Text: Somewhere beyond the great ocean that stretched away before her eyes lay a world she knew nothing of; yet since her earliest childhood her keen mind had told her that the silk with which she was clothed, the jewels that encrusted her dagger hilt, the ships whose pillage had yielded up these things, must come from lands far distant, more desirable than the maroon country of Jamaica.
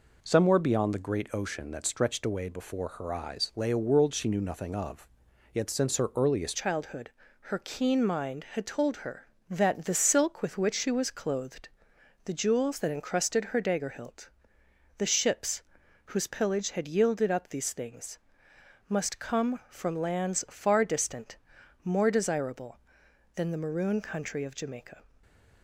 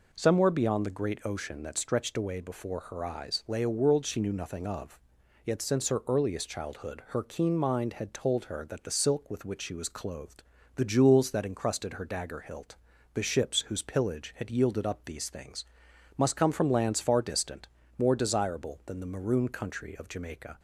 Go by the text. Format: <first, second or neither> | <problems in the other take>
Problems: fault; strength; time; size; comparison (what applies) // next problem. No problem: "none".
second | changes voice at "childhood"; from 6.5 s on; 18.5 s long // pauses between "childhood" and "her"; at 7.0 s; 0.42 s long // pauses between "ships" and "whose"; at 15.6 s; 0.42 s long // stays silent after the last word; slight; from 25.0 s on; 0.6 s long